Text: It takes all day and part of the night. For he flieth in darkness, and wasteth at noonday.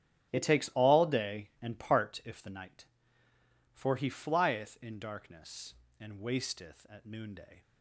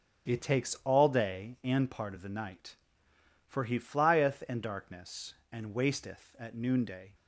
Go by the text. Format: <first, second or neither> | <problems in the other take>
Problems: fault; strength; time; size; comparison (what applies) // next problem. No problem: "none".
second | starts louder than the rest; strong; until 1.3 s; 12.5 dB; strong in the second // says "if" for "of"; at 2.2 s